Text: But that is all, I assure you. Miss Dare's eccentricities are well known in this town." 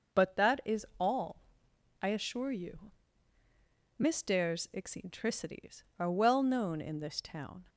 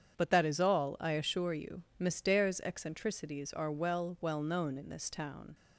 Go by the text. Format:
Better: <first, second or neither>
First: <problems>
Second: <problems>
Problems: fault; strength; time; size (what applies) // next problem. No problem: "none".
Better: first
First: none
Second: starts louder than the rest; strong; until 1.2 s; 8 dB // says "well" twice; at 4.2 s